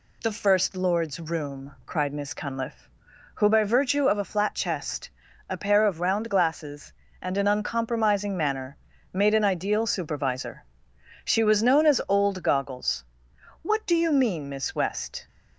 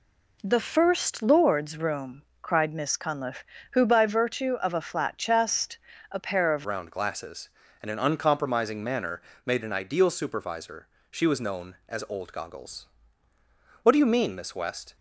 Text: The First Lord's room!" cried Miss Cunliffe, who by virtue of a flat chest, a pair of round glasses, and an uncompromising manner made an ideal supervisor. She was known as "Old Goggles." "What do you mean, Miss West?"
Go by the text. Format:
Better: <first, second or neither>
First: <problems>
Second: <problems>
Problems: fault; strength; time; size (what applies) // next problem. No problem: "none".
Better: first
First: pauses between "manner" and "made"; slight; at 8.7 s; 0.34 s long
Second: changes voice at "round"; from 6.6 s on; 8.3 s long // pauses between "manner" and "made"; slight; at 9.2 s; 0.24 s long